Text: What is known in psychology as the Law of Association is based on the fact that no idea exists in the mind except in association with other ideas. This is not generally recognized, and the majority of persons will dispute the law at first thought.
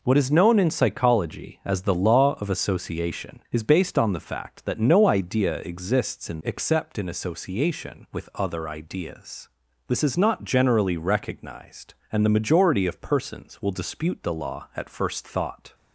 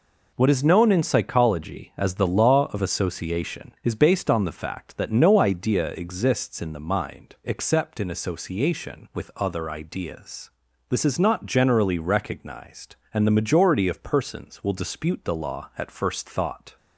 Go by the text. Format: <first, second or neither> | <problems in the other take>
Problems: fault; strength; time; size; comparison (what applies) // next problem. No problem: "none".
second | skips "the mind"; at 6.4 s